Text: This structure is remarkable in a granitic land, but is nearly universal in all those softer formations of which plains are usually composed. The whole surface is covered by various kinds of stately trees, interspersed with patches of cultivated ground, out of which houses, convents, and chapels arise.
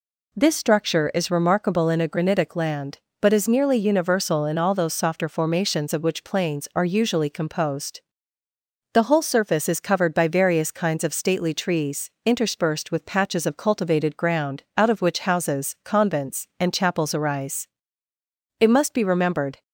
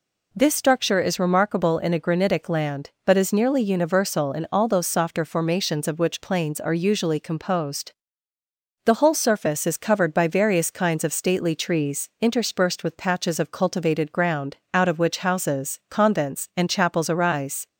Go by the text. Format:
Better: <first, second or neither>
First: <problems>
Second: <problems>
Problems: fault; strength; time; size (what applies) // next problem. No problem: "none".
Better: second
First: goes on to say "It must be remembered"; noticeable; from 18.5 s on; 1.0 s long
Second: none